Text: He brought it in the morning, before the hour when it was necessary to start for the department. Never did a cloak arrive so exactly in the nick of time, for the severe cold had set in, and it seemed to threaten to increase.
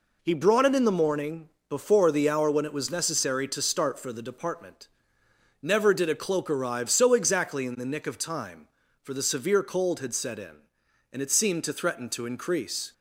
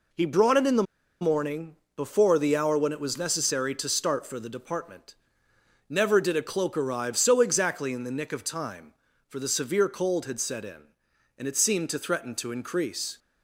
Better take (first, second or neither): first